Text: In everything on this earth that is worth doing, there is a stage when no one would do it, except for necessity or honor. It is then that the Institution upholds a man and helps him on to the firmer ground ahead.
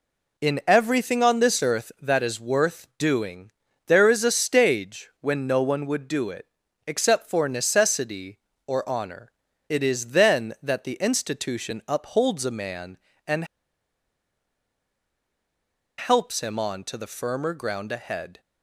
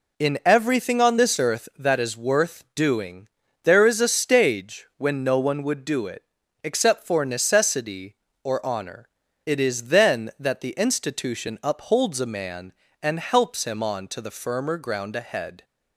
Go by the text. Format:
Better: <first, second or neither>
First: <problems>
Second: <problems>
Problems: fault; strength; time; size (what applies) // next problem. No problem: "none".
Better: second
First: pauses between "and" and "helps"; strong; at 13.4 s; 2.5 s long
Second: none